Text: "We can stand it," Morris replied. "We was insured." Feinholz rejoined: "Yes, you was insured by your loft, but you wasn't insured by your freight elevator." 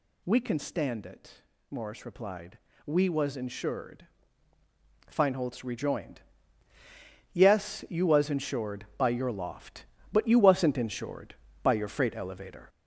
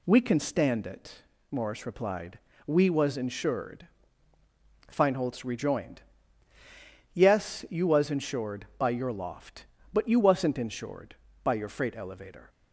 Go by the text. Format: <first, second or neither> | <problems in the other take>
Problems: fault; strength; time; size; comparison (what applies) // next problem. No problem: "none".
second | gets louder; noticeable; throughout; 5.5 dB